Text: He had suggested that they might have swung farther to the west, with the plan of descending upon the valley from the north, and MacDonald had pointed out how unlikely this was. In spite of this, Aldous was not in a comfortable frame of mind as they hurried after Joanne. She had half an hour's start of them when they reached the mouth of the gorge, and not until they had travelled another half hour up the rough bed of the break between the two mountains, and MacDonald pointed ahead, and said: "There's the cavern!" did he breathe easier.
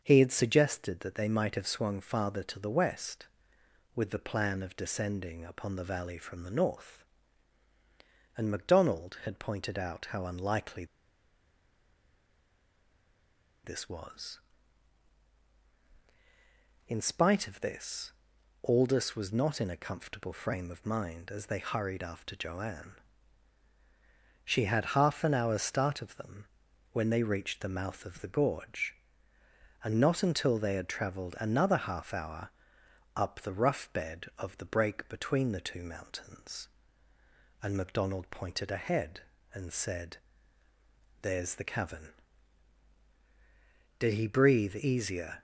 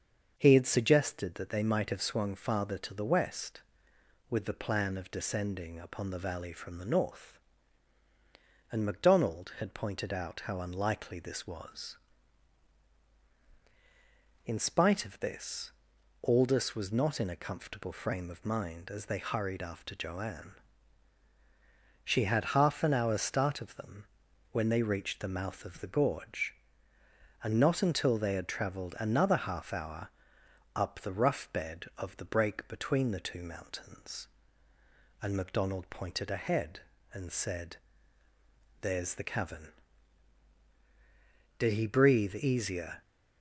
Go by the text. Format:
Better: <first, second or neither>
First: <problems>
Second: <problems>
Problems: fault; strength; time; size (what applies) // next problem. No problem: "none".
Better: second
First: starts louder than the rest; until 1.0 s; 6.5 dB // pauses between "unlikely" and "this"; strong; at 10.8 s; 2.7 s long // pauses between "them" and "when"; noticeable; at 26.4 s; 0.46 s long // pauses between "hour" and "up"; noticeable; at 32.4 s; 0.66 s long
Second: starts louder than the rest; until 1.3 s; 6.5 dB // pauses between "them" and "when"; noticeable; at 24.0 s; 0.46 s long // pauses between "hour" and "up"; noticeable; at 30.0 s; 0.66 s long